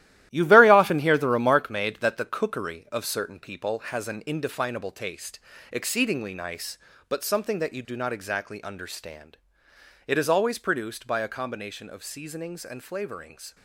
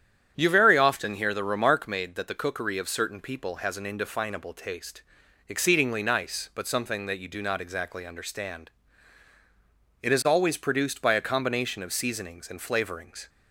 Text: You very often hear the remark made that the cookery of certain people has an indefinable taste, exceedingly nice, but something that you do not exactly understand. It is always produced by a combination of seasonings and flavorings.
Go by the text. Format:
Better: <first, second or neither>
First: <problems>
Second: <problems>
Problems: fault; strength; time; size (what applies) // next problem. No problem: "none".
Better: second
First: gets quieter; strong; throughout; 9 dB // starts louder than the rest; strong; until 1.3 s; 14 dB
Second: starts louder than the rest; strong; until 1.3 s; 9 dB